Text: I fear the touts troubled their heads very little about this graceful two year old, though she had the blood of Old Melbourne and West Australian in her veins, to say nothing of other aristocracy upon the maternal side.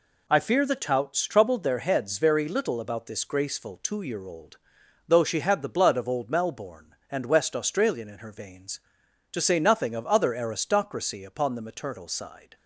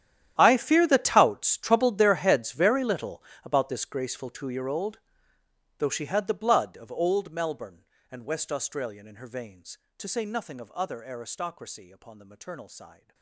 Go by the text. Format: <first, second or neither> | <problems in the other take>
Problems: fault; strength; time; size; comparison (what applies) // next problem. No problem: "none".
first | gets quieter; strong; throughout; 19.5 dB // pauses between "little" and "about"; slight; at 3.2 s; 0.20 s long